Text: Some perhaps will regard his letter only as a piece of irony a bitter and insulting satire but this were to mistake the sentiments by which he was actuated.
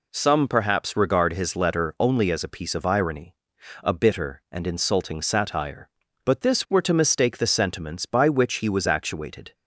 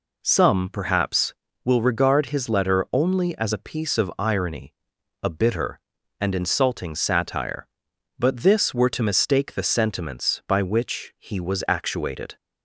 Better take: second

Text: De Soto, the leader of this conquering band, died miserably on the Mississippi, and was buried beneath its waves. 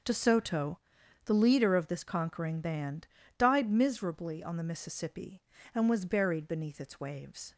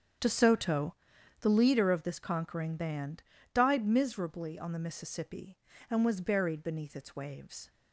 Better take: first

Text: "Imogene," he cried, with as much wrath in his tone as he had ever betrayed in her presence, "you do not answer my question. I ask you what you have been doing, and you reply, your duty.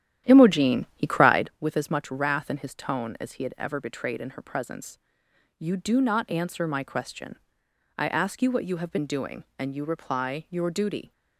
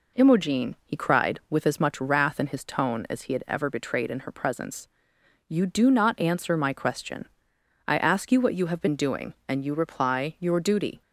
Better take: second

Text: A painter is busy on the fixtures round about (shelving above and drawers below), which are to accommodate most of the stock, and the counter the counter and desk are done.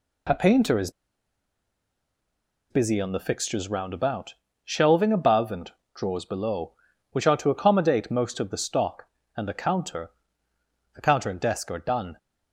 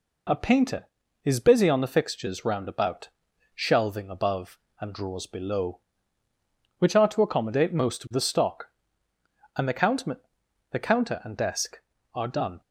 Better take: second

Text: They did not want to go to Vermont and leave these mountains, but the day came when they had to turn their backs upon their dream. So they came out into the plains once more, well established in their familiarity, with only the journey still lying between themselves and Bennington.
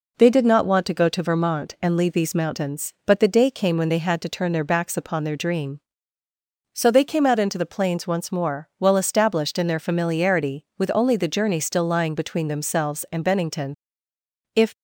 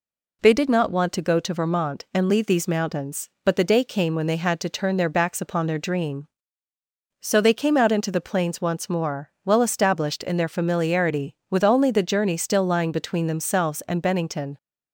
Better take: second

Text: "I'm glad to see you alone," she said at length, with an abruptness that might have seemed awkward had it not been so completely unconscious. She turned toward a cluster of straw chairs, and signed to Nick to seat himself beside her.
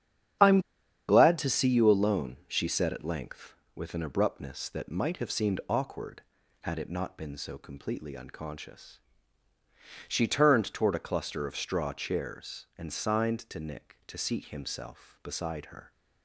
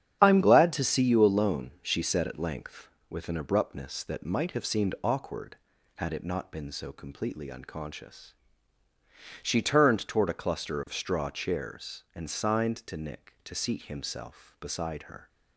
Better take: second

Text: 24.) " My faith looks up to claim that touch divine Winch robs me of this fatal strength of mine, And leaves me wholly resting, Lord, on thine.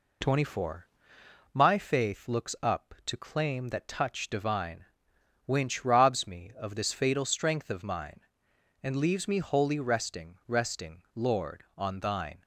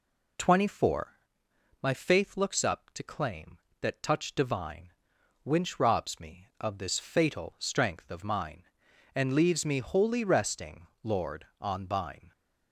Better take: second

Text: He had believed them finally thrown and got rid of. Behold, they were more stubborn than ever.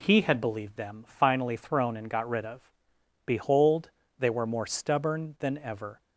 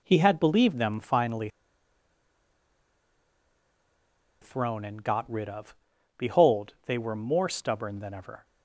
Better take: first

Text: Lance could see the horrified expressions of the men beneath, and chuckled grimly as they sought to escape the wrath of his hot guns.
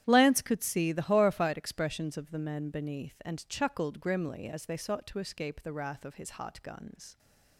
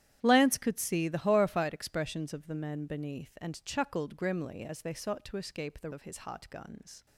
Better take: first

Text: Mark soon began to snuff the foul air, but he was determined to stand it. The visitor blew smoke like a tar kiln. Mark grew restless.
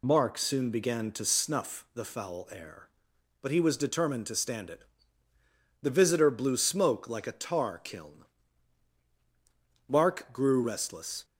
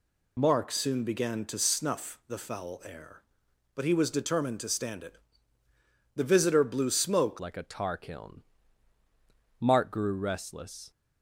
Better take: first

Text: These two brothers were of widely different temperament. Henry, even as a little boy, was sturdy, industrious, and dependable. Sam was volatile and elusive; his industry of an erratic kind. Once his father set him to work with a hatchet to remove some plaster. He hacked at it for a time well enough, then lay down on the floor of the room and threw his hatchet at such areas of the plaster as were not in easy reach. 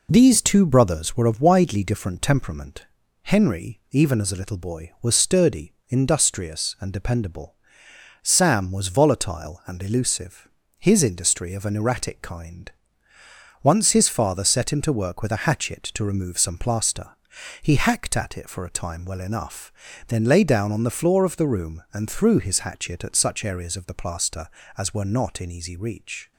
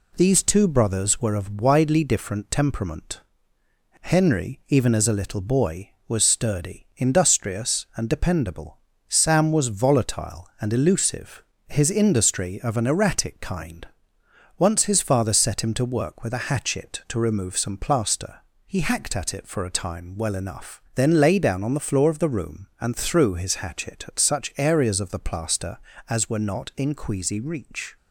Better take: first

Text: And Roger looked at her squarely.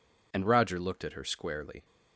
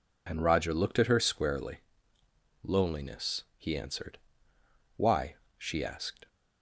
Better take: first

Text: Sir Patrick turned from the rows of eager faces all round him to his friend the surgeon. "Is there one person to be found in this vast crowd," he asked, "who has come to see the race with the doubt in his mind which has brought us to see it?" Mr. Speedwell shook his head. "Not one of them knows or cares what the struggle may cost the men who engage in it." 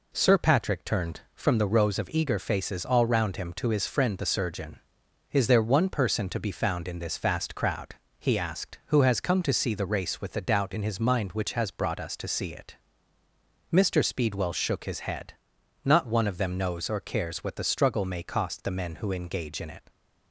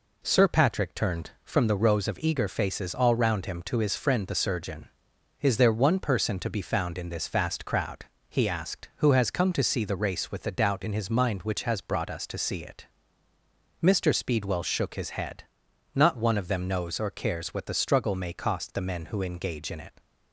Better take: neither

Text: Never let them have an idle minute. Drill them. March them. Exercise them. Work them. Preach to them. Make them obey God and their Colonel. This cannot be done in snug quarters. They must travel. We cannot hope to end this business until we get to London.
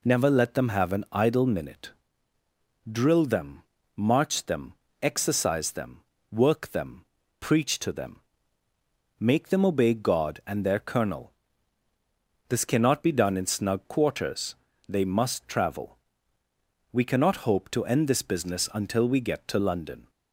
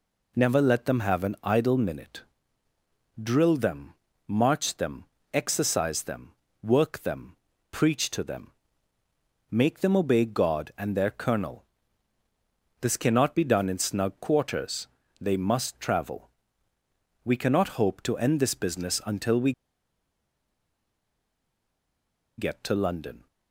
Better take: first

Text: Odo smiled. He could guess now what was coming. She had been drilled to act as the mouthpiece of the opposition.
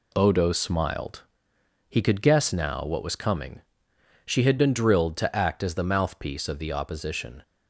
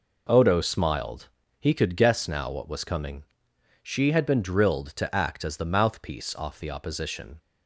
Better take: first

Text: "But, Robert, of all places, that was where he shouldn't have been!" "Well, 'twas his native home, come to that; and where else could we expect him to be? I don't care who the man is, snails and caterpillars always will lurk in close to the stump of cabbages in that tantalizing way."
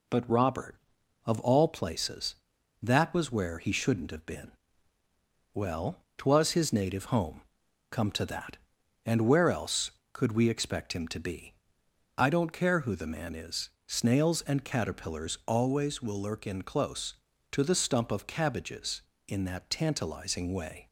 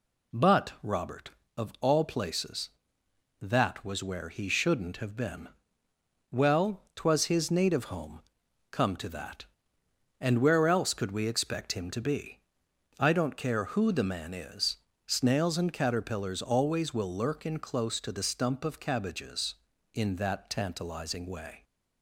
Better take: neither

